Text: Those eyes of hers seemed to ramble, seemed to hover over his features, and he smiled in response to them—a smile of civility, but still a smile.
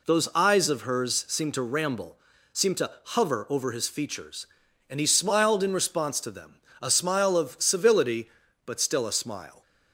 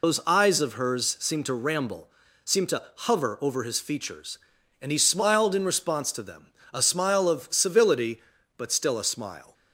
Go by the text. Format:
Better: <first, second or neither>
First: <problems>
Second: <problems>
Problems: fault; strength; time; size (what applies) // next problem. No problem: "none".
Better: first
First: pauses between "to" and "hover"; slight; at 2.8 s; 0.16 s long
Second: loses the start of "Those"; at 0.0 s; 60 ms // pauses between "to" and "hover"; slight; at 2.8 s; 0.16 s long